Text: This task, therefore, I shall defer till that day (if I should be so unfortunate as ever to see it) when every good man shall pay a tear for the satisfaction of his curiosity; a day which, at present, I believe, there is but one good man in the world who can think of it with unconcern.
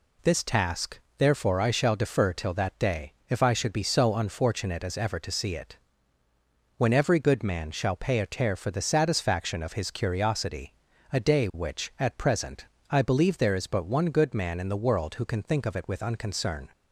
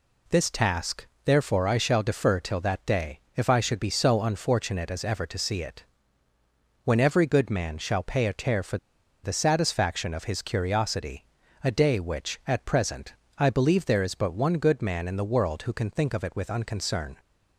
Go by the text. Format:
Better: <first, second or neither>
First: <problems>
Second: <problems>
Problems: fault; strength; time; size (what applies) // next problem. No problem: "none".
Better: first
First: none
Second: pauses between "for" and "the"; noticeable; at 8.7 s; 0.46 s long